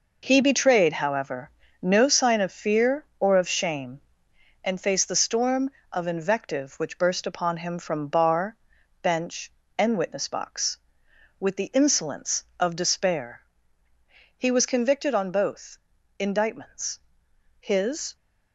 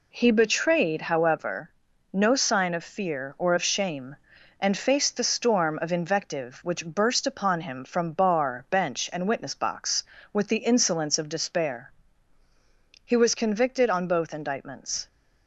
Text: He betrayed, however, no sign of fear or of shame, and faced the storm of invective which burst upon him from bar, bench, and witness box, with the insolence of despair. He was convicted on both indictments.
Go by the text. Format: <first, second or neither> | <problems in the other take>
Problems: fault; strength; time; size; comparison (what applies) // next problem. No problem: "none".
second | pauses between "both" and "indictments"; at 15.7 s; 0.40 s long // goes on to say "His"; from 17.5 s on; 0.56 s long